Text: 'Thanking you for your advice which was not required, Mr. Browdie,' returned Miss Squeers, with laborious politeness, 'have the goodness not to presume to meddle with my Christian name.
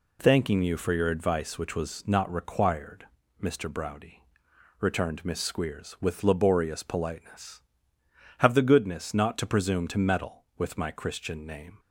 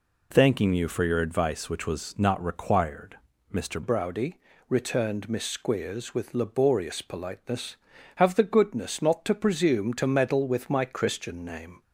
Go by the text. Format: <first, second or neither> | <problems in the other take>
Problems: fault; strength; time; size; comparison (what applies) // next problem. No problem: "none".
first | changes voice at "Browdie"; from 3.8 s on; 8.0 s long